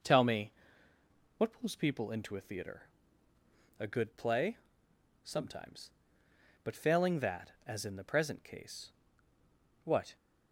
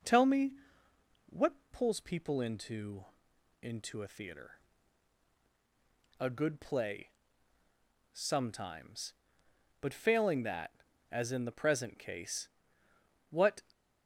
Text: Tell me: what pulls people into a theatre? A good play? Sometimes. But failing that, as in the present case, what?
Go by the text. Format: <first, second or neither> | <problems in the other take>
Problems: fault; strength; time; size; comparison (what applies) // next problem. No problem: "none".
first | pauses between "what" and "pulls"; slight; at 1.5 s; 0.18 s long // says "into" twice; at 3.6 s